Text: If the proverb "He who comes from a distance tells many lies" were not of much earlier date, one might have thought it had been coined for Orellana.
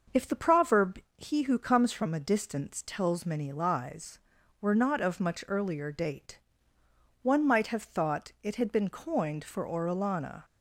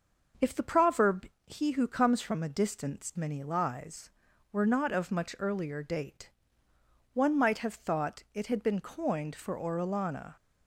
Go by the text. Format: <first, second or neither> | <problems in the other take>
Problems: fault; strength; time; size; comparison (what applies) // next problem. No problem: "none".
first | starts louder than the rest; until 1.6 s; 6 dB // pauses between "proverb" and "He"; slight; at 1.2 s; 0.20 s long; slight in the first // skips "tells"; at 3.1 s